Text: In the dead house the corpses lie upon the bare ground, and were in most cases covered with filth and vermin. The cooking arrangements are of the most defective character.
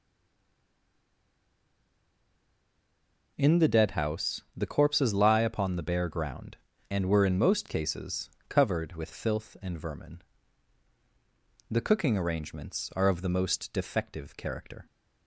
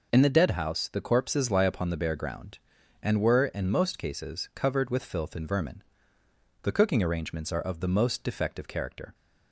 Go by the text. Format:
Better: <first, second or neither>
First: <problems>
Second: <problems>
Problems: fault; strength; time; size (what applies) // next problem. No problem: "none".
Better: second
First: stays silent before the first word; strong; until 3.3 s; 3.3 s long // pauses between "cases" and "covered"; slight; at 8.2 s; 0.18 s long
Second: none